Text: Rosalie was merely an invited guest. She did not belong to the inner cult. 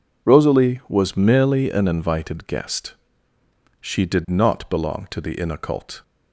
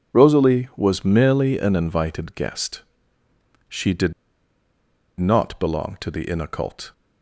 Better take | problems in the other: first | pauses between "did" and "not"; at 4.1 s; 1.0 s long

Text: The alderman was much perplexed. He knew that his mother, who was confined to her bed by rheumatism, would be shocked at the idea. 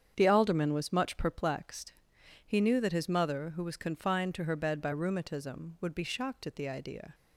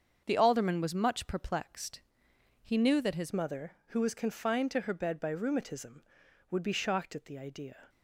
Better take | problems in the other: first | starts louder than the rest; until 1.2 s; 7 dB; strong in the first // changes voice at "mother"; from 3.3 s on; 4.5 s long

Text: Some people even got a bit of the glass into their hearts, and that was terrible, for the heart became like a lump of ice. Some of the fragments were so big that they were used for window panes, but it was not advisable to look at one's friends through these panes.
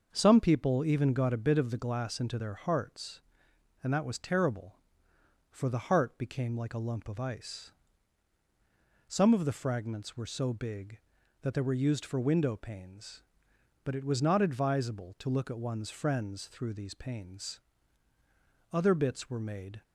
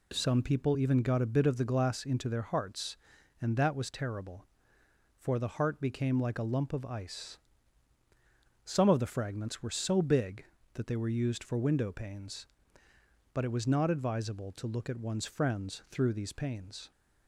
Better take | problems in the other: second | starts louder than the rest; until 1.1 s; 6.5 dB // goes on to say "Other bits were made"; noticeable; from 18.7 s on; 1.1 s long

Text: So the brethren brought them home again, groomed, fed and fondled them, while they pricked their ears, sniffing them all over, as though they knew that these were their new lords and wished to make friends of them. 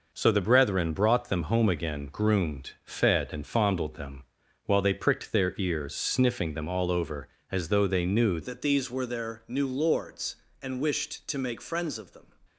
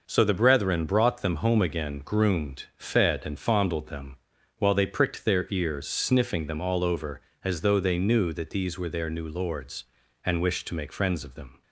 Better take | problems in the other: second | changes voice at "that"; from 8.4 s on; 3.8 s long

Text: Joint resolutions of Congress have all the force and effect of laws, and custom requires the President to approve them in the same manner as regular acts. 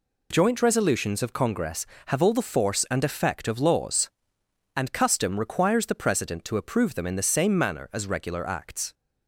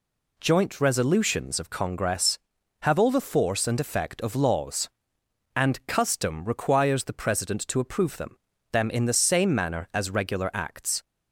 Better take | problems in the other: first | says "them" twice; at 8.7 s

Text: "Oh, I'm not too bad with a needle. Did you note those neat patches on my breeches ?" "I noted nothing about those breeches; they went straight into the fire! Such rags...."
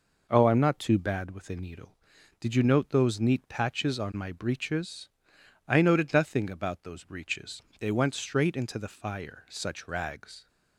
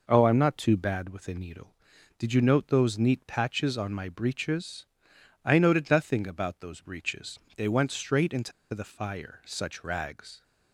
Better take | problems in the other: first | pauses between "into" and "the"; slight; at 8.5 s; 0.21 s long

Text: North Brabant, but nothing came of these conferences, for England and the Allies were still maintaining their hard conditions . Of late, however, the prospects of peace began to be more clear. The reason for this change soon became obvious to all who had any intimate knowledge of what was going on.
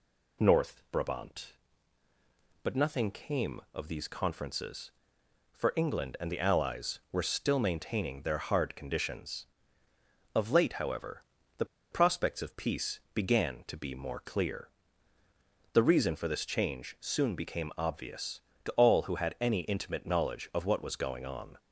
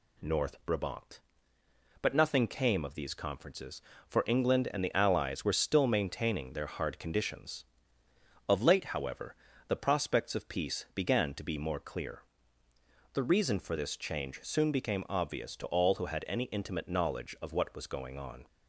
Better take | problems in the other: second | pauses between "the" and "prospects"; slight; at 11.6 s; 0.27 s long

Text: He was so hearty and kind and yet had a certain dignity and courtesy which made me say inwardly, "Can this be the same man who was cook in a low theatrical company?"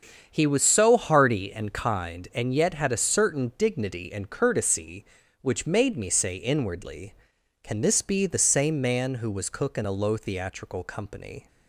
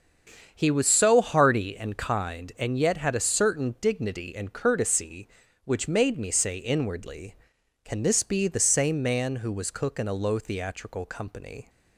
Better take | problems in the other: neither | starts louder than the rest; strong; the same in both

